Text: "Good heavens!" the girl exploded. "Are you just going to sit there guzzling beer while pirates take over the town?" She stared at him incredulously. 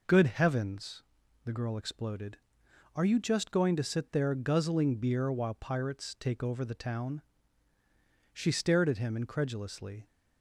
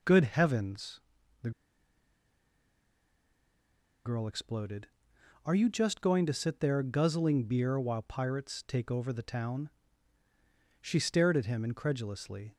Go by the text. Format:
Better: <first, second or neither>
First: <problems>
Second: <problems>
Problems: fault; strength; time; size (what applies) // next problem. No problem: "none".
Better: first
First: none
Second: pauses between "the" and "girl"; strong; at 1.5 s; 2.5 s long